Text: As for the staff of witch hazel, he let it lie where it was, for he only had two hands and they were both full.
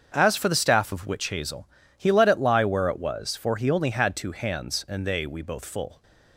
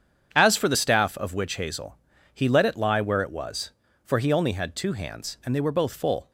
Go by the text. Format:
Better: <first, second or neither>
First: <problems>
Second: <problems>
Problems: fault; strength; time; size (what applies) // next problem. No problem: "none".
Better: second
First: starts louder than the rest; strong; until 1.1 s; 7 dB // says "we" for "were"; at 5.2 s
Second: starts louder than the rest; strong; until 1.3 s; 8 dB